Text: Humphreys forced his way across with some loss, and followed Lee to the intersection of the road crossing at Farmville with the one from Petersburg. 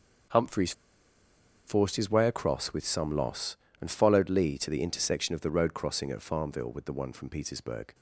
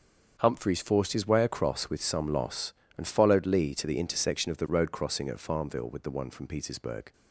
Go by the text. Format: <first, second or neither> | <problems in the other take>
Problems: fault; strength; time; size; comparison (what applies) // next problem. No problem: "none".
second | starts louder than the rest; until 2.2 s; 7 dB; also in the second // pauses between "Humphreys" and "forced"; noticeable; at 0.7 s; 0.94 s long